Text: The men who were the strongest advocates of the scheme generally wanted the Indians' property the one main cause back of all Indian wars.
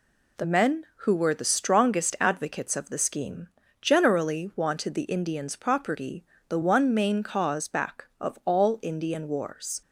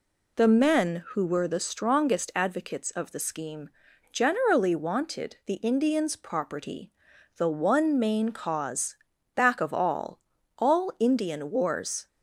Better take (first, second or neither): first